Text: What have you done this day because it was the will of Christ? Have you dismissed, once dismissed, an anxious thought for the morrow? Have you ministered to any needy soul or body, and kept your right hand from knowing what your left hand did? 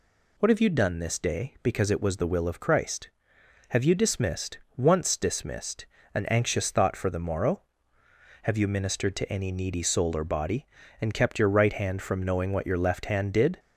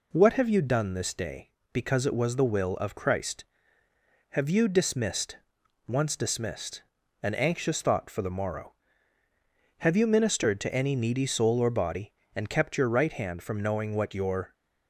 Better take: first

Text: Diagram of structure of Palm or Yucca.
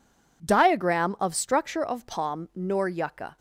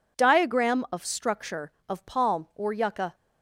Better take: second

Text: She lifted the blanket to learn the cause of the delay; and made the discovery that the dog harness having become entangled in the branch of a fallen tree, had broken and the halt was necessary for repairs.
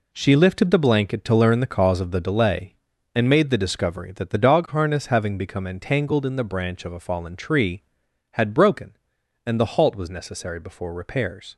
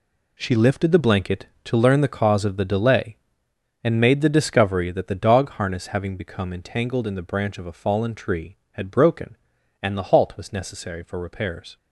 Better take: second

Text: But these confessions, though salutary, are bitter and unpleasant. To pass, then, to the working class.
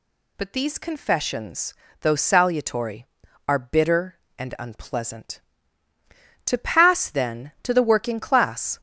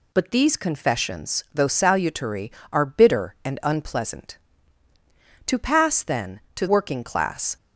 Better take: first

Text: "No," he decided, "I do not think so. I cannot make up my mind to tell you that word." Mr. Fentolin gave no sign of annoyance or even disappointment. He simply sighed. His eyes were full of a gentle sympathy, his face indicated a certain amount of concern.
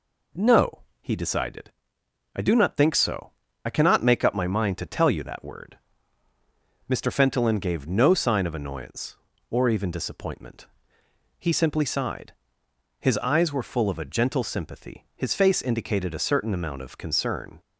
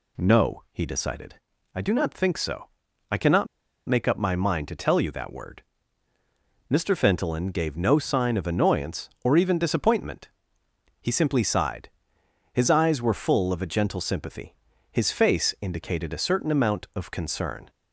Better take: first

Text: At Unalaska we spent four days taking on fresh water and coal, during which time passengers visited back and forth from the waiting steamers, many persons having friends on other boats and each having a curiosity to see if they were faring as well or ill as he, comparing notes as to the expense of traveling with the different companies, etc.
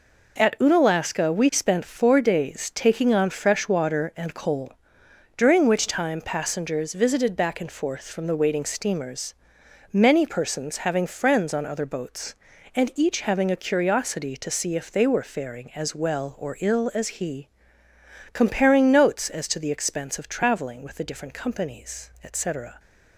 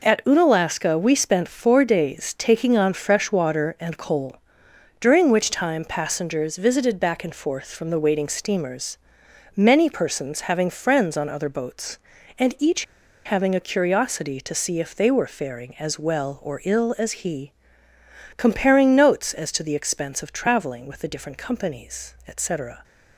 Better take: first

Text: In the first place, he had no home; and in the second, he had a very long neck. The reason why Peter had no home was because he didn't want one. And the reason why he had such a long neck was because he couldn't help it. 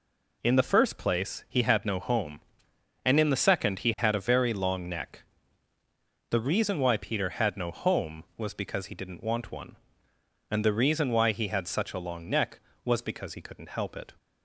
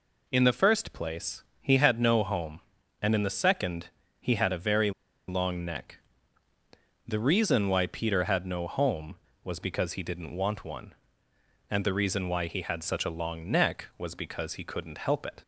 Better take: first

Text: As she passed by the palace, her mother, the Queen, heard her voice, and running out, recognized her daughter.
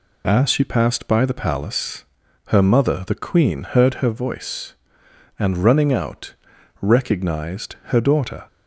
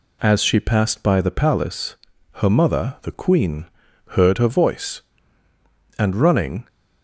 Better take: first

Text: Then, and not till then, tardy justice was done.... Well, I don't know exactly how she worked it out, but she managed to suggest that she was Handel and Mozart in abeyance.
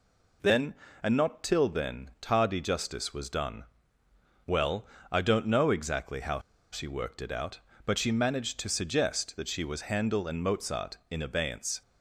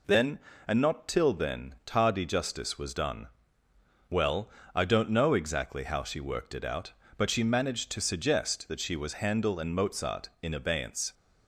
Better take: second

